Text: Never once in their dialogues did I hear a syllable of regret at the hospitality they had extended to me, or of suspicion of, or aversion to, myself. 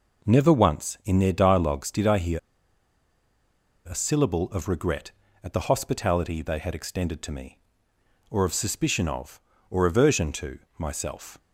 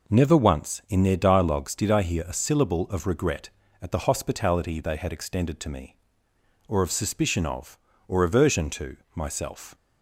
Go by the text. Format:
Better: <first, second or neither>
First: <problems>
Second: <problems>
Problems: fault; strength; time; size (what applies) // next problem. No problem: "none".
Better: second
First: pauses between "hear" and "a"; strong; at 2.3 s; 1.5 s long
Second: none